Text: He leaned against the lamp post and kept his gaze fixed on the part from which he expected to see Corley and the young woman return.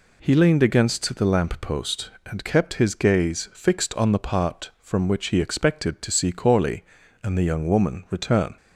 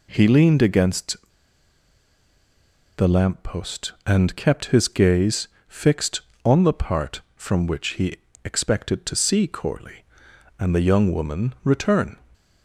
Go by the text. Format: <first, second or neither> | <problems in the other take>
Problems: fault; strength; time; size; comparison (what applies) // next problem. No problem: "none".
first | pauses between "against" and "the"; strong; at 1.1 s; 1.7 s long // pauses between "gaze" and "fixed"; slight; at 5.4 s; 0.20 s long // pauses between "he" and "expected"; slight; at 8.1 s; 0.30 s long